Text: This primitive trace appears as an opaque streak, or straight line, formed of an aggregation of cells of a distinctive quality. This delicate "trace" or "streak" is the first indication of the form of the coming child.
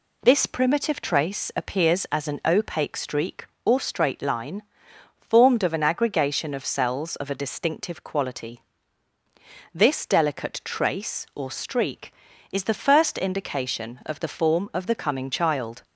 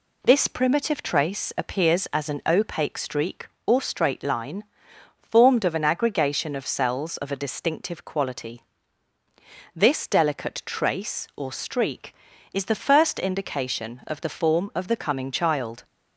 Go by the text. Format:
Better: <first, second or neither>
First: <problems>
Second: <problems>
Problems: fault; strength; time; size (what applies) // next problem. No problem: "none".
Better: neither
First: none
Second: none